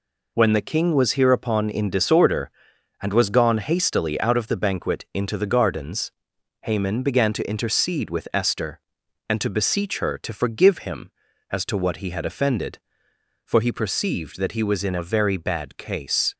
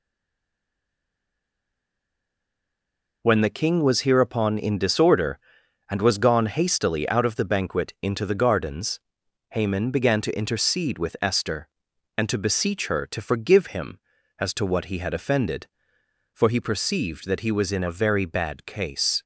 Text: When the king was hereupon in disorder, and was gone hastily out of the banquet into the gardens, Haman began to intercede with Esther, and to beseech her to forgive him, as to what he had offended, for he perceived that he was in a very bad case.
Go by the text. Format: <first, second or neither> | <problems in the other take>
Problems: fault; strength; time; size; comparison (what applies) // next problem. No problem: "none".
first | stays silent before the first word; strong; until 3.2 s; 3.2 s long